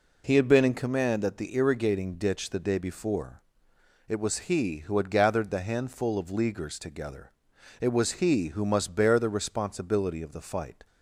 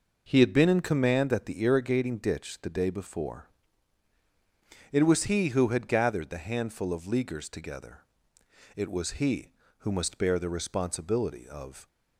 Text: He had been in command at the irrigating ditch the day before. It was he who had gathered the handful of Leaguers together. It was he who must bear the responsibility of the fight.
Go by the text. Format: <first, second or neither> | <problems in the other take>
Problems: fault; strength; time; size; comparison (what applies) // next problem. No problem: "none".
first | stops before "the fight"; at 11.8 s